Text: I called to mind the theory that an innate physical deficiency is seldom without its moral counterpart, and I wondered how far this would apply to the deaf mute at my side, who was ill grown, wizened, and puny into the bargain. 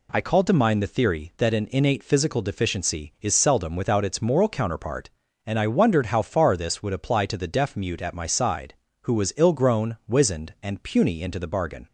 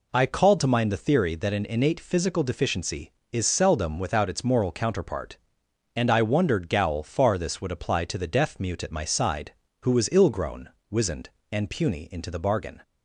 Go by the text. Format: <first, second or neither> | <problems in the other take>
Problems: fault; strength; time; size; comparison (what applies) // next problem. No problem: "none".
first | says "gowl" for "how"; at 6.6 s